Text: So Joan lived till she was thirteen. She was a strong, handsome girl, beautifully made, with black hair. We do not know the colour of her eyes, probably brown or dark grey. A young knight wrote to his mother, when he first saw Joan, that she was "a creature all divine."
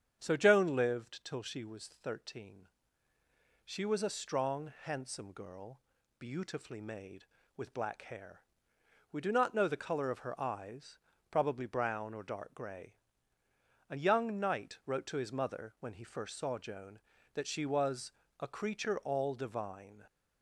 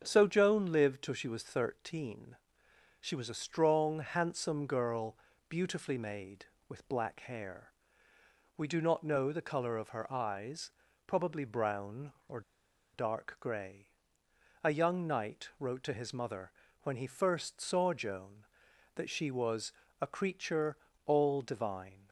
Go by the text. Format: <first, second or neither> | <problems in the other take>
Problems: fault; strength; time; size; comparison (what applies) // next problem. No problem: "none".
first | starts louder than the rest; strong; until 1.0 s; 7.5 dB; strong in the first // pauses between "or" and "dark"; noticeable; at 12.4 s; 0.53 s long // pauses between "was" and "a"; slight; at 19.7 s; 0.30 s long; slight in the first // pauses between "creature" and "all"; slight; at 20.7 s; 0.30 s long